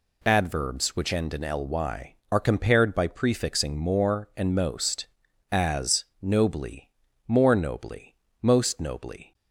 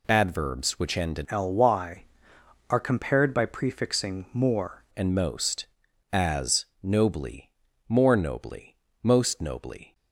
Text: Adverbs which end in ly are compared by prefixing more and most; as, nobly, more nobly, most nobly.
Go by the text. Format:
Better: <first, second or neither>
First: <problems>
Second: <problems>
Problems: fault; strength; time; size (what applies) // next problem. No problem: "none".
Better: first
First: none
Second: changes voice from "ly" to "more"; from 1.2 to 4.8 s; 3.6 s long